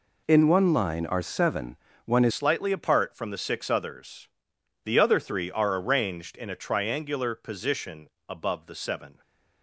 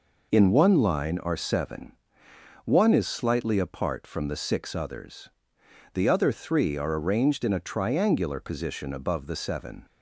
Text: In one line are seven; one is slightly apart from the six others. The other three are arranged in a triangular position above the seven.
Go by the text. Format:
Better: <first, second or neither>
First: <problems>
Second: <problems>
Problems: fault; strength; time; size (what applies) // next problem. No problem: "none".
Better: second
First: changes voice at "slightly"; from 2.3 s on; 6.9 s long // pauses between "position" and "above"; slight; at 8.0 s; 0.18 s long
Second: none